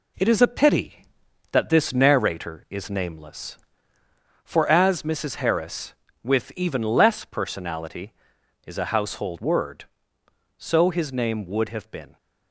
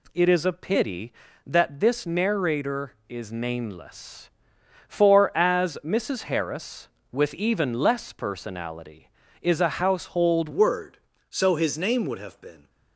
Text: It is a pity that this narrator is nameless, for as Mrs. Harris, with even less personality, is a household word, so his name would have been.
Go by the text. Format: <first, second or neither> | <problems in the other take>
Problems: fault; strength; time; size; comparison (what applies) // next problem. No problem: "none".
first | changes voice at "word"; from 10.5 s on; 2.1 s long